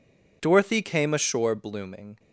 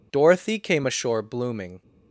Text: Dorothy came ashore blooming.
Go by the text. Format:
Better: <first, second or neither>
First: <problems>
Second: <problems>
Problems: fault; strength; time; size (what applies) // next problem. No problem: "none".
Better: neither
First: none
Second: none